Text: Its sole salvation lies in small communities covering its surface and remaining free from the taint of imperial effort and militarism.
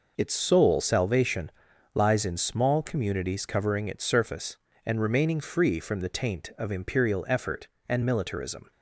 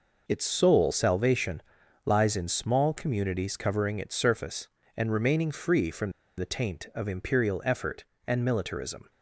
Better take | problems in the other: first | pauses between "salvation" and "lies"; at 1.6 s; 0.44 s long; also in the first // pauses between "from" and "the"; slight; at 6.1 s; 0.26 s long

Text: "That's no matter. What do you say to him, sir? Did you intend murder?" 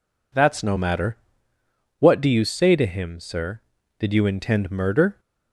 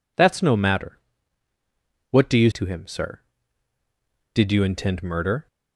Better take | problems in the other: first | skips "say"; at 2.5 s

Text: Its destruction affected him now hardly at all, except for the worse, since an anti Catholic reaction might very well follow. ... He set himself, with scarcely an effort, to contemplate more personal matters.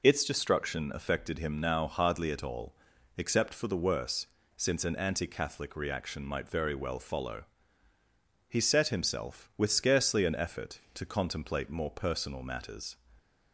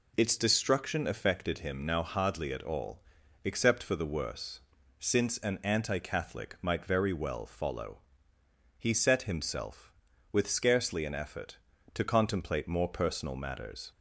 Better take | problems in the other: first | skips "reaction"; at 6.5 s

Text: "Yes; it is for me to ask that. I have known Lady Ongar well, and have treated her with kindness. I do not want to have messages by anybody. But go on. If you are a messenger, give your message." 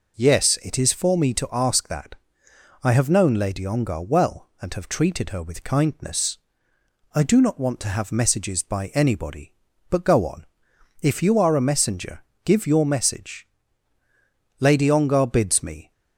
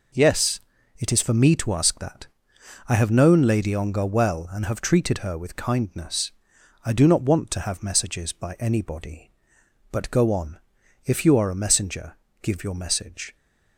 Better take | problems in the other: second | goes on to say "Lady Ongar bids me"; noticeable; from 14.6 s on; 1.3 s long

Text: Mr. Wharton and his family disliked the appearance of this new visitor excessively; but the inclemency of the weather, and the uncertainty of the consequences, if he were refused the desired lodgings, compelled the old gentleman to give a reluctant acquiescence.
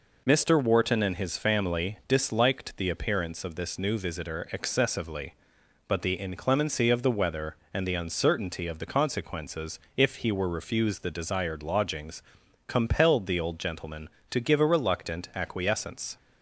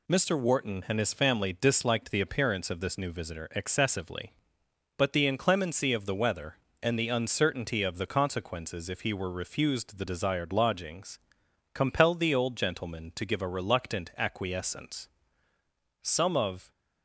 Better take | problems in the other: first | goes on to say "Some of"; noticeable; from 16.0 s on; 0.68 s long

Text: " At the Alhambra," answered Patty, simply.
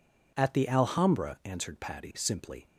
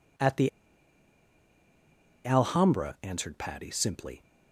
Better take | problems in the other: first | pauses between "the" and "Alhambra"; strong; at 0.4 s; 1.7 s long

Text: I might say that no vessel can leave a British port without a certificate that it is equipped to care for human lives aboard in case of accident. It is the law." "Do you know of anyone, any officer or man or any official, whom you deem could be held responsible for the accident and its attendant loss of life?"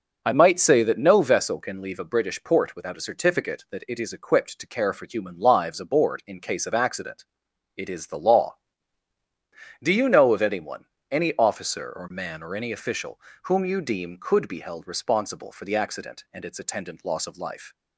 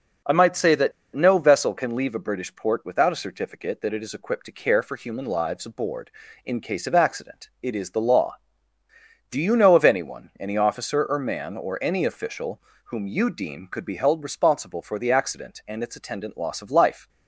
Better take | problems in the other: first | pauses between "that" and "no"; slight; at 0.9 s; 0.22 s long

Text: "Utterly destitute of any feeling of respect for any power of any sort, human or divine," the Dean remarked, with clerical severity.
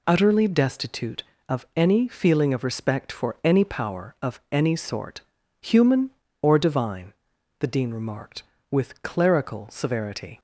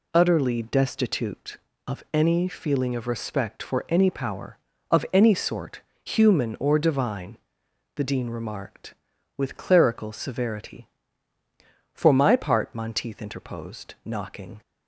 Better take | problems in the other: first | goes on to say "For my part Monteith interposed knocking"; strong; from 11.9 s on; 2.6 s long

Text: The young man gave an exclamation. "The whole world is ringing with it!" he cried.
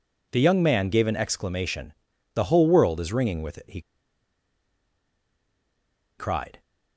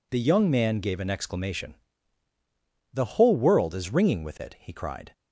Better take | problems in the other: second | pauses between "he" and "cried"; strong; at 3.8 s; 2.3 s long

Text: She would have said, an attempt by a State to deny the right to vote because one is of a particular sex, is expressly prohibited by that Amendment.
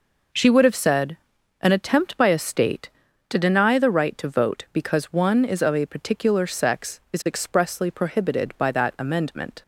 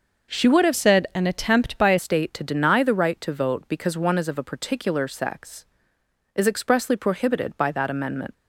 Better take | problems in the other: first | changes voice from "said" to "a"; from 0.7 to 1.9 s; 1.2 s long

